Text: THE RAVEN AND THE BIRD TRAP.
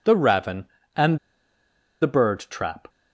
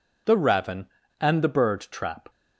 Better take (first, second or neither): second